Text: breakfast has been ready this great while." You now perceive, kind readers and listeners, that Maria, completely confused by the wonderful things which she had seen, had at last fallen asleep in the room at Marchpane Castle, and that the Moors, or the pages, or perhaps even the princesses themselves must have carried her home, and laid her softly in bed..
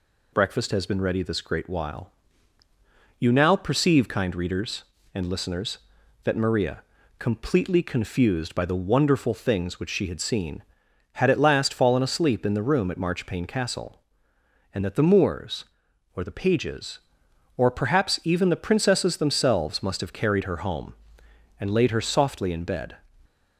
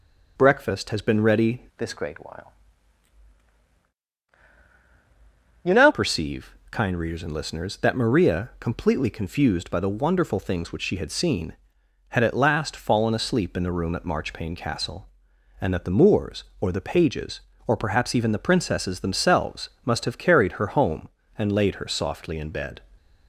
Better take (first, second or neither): first